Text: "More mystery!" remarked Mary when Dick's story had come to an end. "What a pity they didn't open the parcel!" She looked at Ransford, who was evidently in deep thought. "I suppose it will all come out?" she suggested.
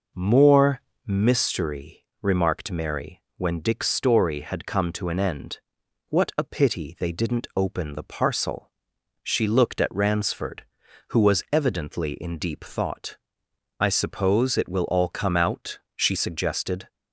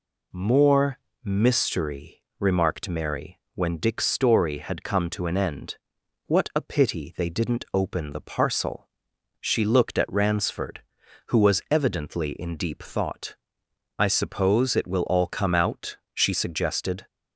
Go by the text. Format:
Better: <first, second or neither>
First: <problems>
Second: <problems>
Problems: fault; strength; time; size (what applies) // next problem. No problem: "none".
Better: second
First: starts louder than the rest; noticeable; until 1.3 s; 5 dB // pauses between "More" and "mystery"; slight; at 0.8 s; 0.26 s long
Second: pauses between "More" and "mystery"; slight; at 0.9 s; 0.26 s long